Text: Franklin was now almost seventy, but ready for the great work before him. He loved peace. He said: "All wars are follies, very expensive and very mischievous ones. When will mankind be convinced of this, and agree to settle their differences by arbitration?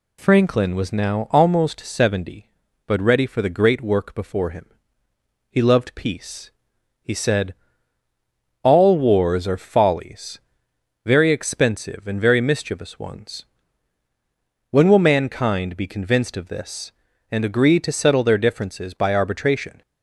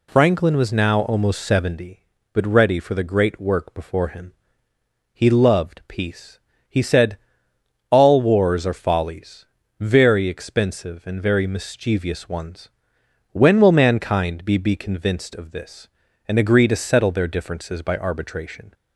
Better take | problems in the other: first | says "be" twice; at 14.5 s

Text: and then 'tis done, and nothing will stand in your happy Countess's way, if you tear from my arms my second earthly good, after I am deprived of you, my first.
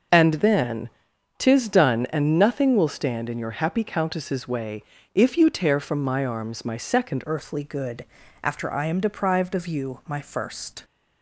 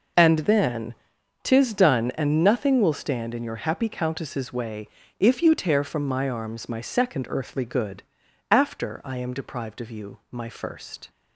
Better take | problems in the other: second | pauses between "then" and "tis"; noticeable; at 0.8 s; 0.48 s long; noticeable in the second // changes voice at "earthly"; from 7.2 s on; 3.6 s long

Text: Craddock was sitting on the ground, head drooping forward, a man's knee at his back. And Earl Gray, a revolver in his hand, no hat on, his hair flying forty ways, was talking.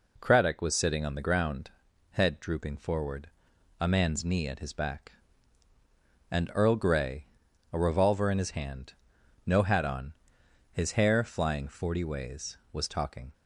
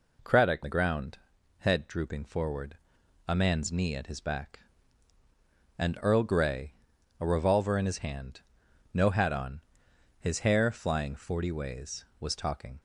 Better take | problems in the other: first | skips "was sitting on"; at 0.6 s

